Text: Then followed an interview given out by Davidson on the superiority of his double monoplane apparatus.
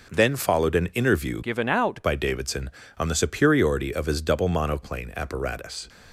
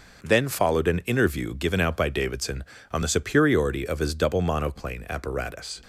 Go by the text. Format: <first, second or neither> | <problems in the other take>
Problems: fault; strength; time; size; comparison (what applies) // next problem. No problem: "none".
second | changes voice from "given" to "out"; from 1.4 to 2.0 s; 0.6 s long